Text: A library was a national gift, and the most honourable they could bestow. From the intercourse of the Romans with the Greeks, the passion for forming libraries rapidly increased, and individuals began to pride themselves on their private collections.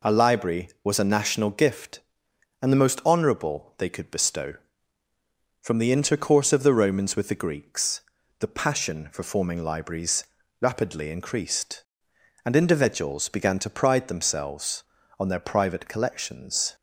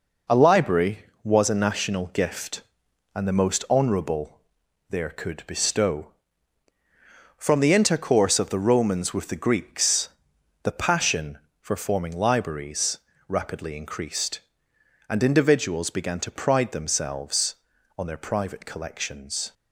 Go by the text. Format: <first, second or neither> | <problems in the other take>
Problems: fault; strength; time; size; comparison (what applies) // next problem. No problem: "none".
first | says "there" for "they"; at 4.8 s // pauses between "libraries" and "rapidly"; slight; at 12.9 s; 0.32 s long; slight in the first